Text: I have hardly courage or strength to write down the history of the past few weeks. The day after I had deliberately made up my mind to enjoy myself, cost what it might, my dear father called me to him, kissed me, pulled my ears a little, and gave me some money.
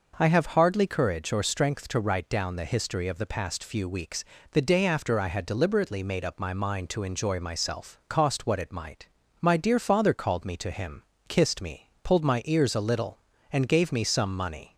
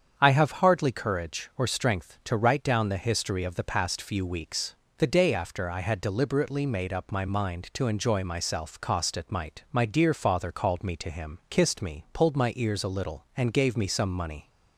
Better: first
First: none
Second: starts louder than the rest; strong; until 1.1 s; 7.5 dB // skips "what"; at 9.1 s

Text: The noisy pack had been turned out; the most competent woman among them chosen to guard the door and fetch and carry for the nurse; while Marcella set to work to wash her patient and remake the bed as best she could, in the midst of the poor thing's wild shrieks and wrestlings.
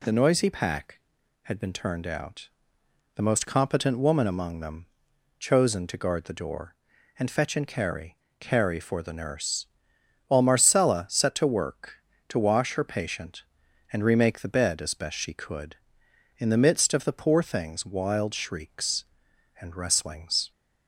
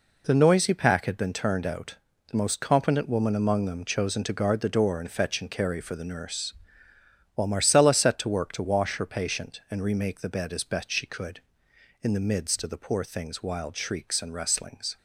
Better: second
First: pauses between "them" and "chosen"; noticeable; at 4.8 s; 0.52 s long // says "carry" twice; at 8.3 s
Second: none

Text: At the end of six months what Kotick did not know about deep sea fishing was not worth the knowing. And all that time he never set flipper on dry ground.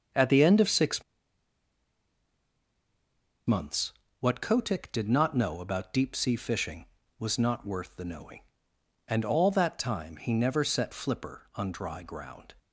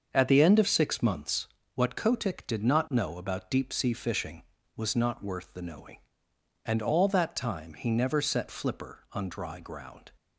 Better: second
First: starts louder than the rest; until 3.5 s; 6.5 dB // pauses between "six" and "months"; strong; at 1.0 s; 2.4 s long // pauses between "months" and "what"; slight; at 3.9 s; 0.28 s long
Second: starts louder than the rest; until 1.1 s; 6.5 dB // pauses between "months" and "what"; slight; at 1.4 s; 0.28 s long

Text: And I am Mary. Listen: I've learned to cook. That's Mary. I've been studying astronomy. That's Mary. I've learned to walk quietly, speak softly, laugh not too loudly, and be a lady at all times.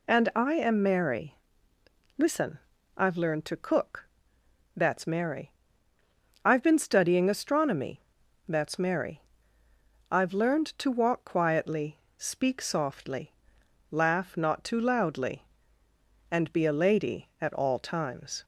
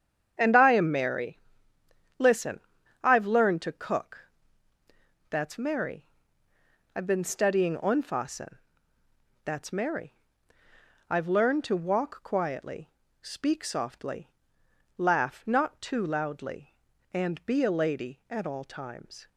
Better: first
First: none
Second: starts louder than the rest; strong; until 1.3 s; 8 dB // says "onfassen" for "astronomy"; at 7.7 s

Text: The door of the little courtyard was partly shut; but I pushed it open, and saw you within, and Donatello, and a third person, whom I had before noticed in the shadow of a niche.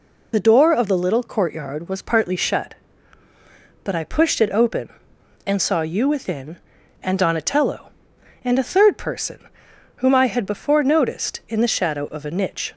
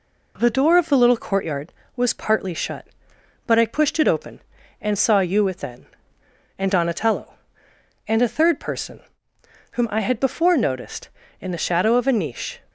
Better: second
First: loses the start of "The"; at 0.3 s; 35 ms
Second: none

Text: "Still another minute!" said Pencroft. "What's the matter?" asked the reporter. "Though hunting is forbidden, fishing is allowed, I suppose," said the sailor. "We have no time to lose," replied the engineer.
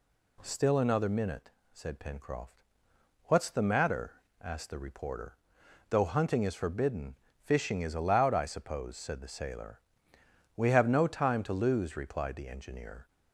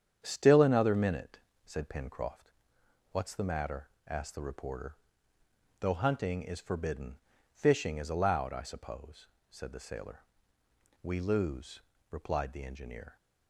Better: first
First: none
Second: starts louder than the rest; strong; until 1.2 s; 8.5 dB // skips "have no time to"; at 11.1 s

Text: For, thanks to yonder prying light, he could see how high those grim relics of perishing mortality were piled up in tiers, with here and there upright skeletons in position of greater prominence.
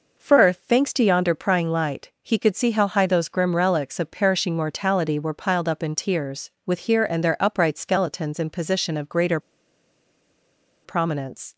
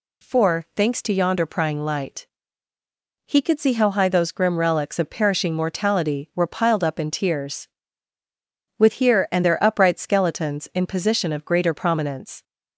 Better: second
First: pauses between "greater" and "prominence"; strong; at 9.3 s; 1.4 s long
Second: none

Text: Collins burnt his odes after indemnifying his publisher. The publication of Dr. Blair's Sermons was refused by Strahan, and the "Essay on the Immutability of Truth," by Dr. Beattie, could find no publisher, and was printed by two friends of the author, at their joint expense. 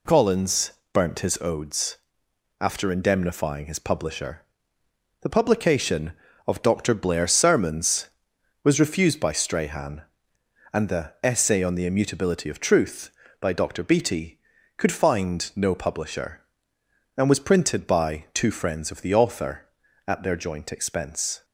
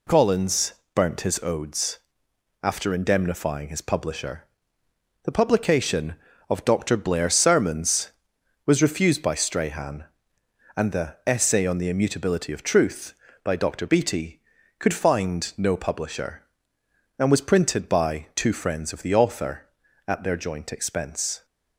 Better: neither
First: pauses between "Collins" and "burnt"; slight; at 0.7 s; 0.22 s long // pauses between "odes" and "after"; noticeable; at 1.9 s; 0.65 s long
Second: pauses between "Collins" and "burnt"; slight; at 0.7 s; 0.22 s long // pauses between "odes" and "after"; noticeable; at 1.9 s; 0.66 s long

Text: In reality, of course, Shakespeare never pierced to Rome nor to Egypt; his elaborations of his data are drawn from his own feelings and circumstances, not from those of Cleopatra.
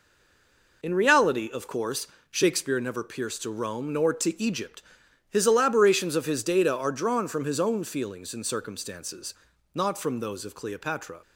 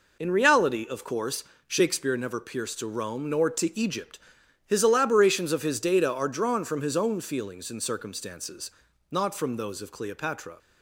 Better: second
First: stays silent before the first word; slight; until 0.8 s; 0.8 s long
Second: none

